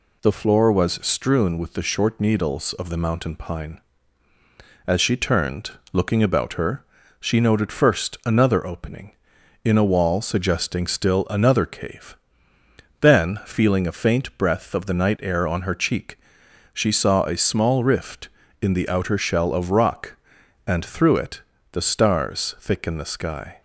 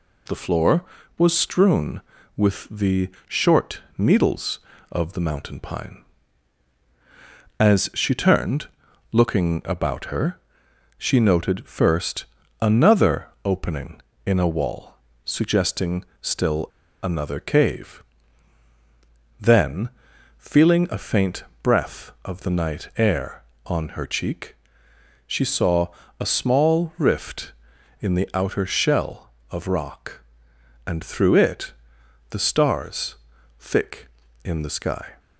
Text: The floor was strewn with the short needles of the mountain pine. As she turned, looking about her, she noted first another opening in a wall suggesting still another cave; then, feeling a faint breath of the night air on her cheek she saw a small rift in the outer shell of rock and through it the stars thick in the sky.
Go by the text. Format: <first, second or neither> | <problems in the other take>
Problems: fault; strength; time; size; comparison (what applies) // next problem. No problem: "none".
first | pauses between "the" and "short"; slight; at 3.0 s; 0.18 s long // pauses between "short" and "needles"; slight; at 3.8 s; 0.16 s long // pauses between "first" and "another"; slight; at 12.2 s; 0.36 s long // pauses between "another" and "opening"; slight; at 13.2 s; 0.16 s long // pauses between "wall" and "suggesting"; slight; at 14.9 s; 0.32 s long // pauses between "suggesting" and "still"; slight; at 16.0 s; 0.16 s long // pauses between "still" and "another"; at 16.6 s; 0.36 s long // pauses between "faint" and "breath"; slight; at 21.4 s; 0.20 s long // pauses between "cheek" and "she"; noticeable; at 24.5 s; 0.72 s long; noticeable in the first // pauses between "saw" and "a"; slight; at 25.8 s; 0.32 s long // pauses between "it" and "the"; noticeable; at 31.7 s; 0.56 s long; slight in the first // pauses between "stars" and "thick"; at 33.1 s; 0.44 s long